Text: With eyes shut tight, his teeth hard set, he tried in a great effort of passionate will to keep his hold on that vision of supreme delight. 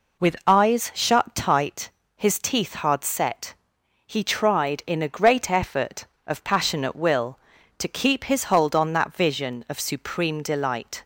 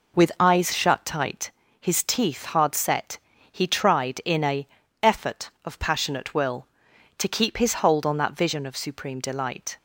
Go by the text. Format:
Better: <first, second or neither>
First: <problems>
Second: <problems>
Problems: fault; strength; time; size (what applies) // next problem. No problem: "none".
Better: first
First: none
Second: skips "great"; at 4.8 s